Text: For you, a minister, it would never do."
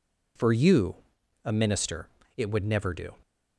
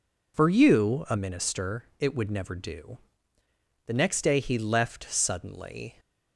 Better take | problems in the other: first | goes on to say "The next day he left suddenly"; strong; from 3.8 s on; 2.1 s long

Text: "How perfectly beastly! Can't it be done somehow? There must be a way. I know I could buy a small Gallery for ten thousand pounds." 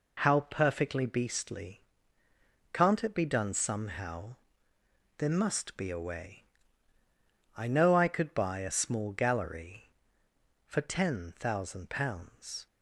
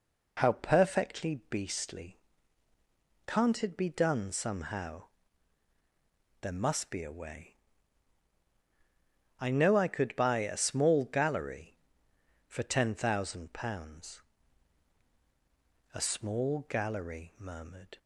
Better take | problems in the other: first | goes on to say "A small Gallery murmured"; strong; from 15.9 s on; 2.0 s long

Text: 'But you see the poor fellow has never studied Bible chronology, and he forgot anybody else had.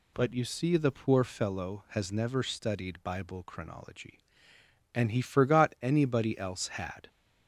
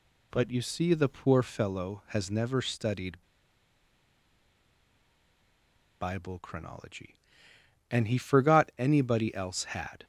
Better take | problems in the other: first | pauses between "studied" and "Bible"; strong; at 3.2 s; 2.7 s long

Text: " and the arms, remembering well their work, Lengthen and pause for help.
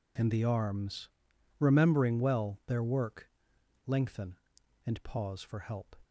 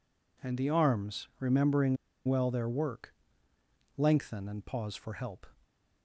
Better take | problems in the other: first | pauses between "remembering" and "well"; slight; at 1.9 s; 0.30 s long

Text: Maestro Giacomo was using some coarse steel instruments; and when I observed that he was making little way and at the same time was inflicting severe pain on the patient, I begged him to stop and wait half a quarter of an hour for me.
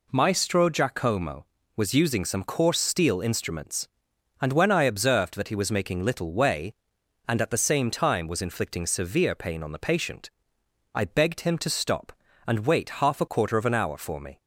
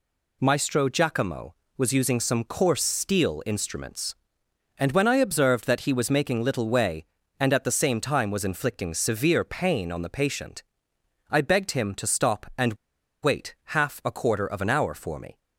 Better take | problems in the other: first | pauses between "and" and "wait"; noticeable; at 12.7 s; 0.48 s long

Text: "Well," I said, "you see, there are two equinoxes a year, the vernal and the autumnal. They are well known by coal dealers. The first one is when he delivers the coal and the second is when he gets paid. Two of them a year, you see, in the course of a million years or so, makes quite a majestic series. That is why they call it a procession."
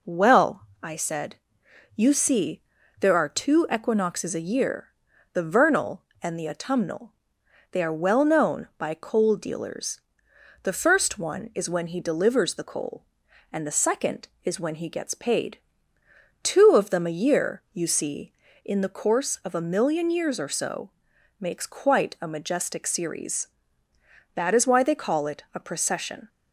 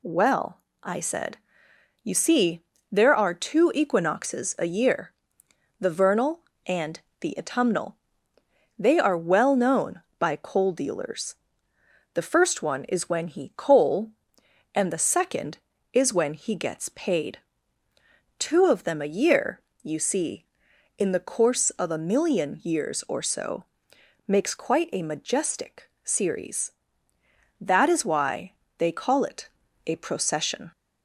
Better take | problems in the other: first | pauses between "and" and "the"; slight; at 7.0 s; 0.20 s long // skips "delivers the"; at 13.5 s // pauses between "why" and "they"; slight; at 28.5 s; 0.24 s long // pauses between "it" and "a"; at 29.4 s; 0.40 s long

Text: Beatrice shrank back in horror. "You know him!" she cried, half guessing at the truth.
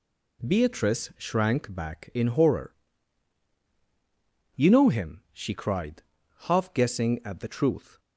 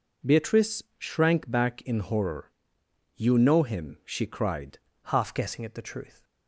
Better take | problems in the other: first | pauses between "Beatrice" and "shrank"; slight; at 0.8 s; 0.16 s long // changes voice at "half"; from 5.0 s on; 1.2 s long

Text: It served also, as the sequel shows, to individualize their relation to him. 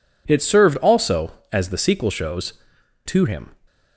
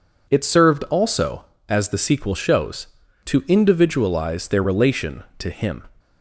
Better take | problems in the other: second | skips "to individualize their relation"; at 2.7 s

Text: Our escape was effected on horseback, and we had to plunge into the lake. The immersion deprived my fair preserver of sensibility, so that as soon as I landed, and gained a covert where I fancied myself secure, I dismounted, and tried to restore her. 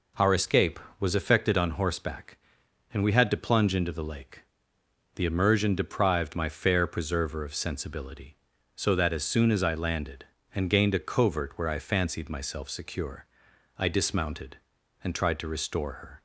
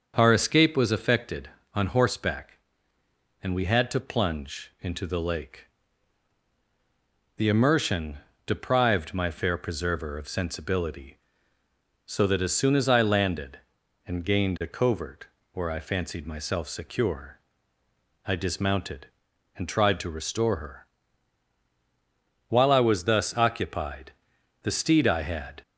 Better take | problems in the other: first | starts louder than the rest; until 1.1 s; 7 dB // pauses between "immersion" and "deprived"; slight; at 8.1 s; 0.28 s long // pauses between "covert" and "where"; slight; at 15.2 s; 0.24 s long // goes on to say "While I was thus occupied the steed I had"; strong; from 22.4 s on; 3.1 s long

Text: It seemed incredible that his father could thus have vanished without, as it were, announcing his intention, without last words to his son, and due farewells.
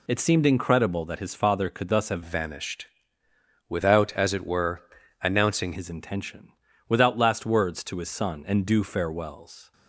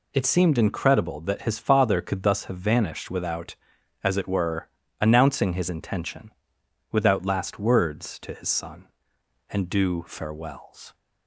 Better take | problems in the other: second | changes voice from "vanished" to "announcing"; from 2.2 to 5.7 s; 3.5 s long // pauses between "vanished" and "without"; noticeable; at 2.8 s; 0.84 s long

